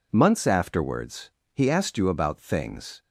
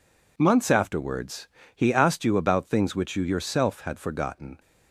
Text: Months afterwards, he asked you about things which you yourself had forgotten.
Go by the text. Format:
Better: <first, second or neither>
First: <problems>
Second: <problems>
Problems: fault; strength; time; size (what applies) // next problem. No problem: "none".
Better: second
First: stops before "which you yourself had forgotten"; at 3.0 s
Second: none